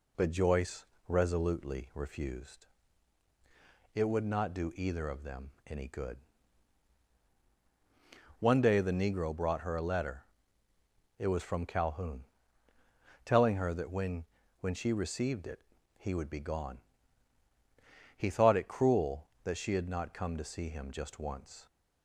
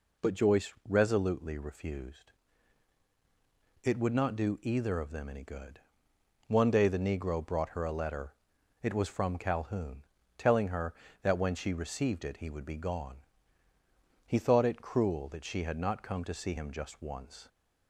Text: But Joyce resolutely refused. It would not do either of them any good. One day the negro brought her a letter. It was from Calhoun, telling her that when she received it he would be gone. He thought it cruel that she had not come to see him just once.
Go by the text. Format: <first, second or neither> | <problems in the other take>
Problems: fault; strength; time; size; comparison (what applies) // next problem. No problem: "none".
second | pauses between "Joyce" and "resolutely"; slight; at 0.8 s; 0.24 s long // pauses between "them" and "any"; slight; at 5.5 s; 0.16 s long // says "when" twice; at 14.5 s // pauses between "it" and "he"; at 15.5 s; 0.38 s long